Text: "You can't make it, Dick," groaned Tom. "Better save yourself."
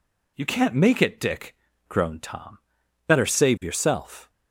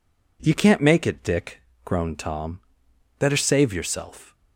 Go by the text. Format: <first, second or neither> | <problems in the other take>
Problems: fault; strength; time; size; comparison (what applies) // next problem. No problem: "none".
neither | none